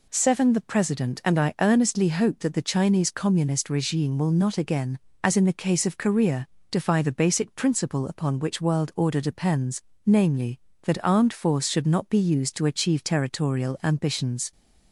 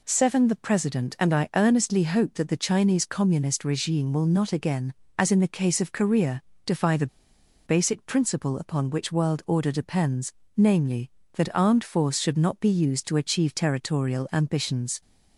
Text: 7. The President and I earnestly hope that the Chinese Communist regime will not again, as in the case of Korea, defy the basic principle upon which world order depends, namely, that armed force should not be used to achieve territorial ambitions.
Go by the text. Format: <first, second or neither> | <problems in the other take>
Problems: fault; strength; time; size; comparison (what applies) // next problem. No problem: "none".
first | pauses between "the" and "basic"; noticeable; at 7.0 s; 0.59 s long